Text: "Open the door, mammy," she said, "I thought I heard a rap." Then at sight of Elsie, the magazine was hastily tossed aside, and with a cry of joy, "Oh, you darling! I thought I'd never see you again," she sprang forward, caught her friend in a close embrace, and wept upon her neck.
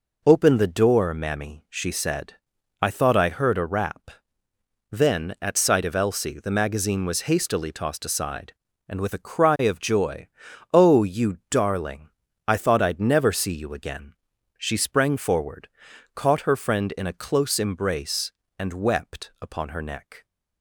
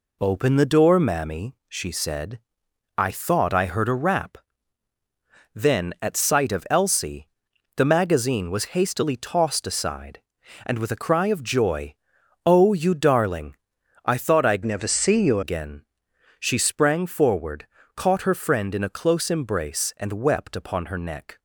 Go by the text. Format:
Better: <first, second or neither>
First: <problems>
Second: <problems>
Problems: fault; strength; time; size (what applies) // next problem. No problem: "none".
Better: first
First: none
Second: changes voice from "never" to "you"; from 14.6 to 15.4 s; 0.8 s long